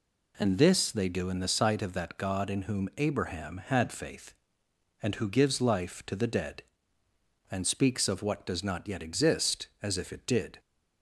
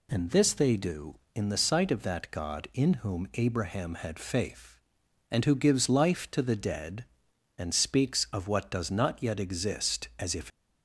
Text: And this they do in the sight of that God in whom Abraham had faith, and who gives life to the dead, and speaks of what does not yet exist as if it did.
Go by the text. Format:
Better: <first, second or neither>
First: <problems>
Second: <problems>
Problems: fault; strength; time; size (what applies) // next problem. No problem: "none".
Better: first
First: none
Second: stops before "it did"; at 10.5 s